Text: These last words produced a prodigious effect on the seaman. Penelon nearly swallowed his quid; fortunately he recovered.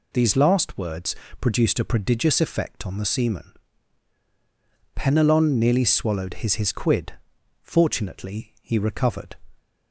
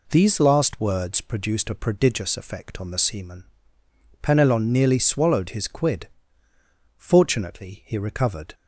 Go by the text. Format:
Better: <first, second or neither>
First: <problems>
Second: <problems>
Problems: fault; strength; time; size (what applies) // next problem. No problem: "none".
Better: second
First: pauses between "words" and "produced"; slight; at 1.1 s; 0.24 s long // says "his" twice; at 6.5 s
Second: none